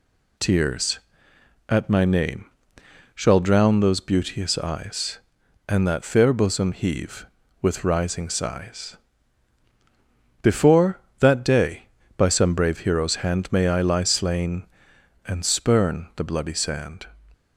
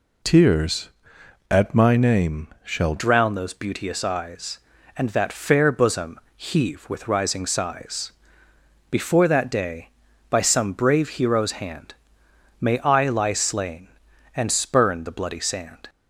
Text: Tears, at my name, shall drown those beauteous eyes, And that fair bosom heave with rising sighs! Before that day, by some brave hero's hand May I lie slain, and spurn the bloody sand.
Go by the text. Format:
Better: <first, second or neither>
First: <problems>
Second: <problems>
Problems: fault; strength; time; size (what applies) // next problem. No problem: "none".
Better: first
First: none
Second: changes voice at "drown"; from 2.9 s on; 12.9 s long // pauses between "bosom" and "heave"; slight; at 6.1 s; 0.18 s long // pauses between "hand" and "May"; noticeable; at 11.9 s; 0.66 s long